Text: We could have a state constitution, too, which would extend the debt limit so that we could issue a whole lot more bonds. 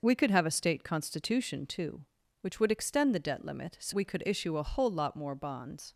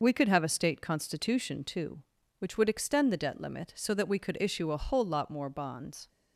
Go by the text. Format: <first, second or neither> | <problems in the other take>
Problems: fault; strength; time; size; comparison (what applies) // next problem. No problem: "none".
second | skips "that"; at 3.9 s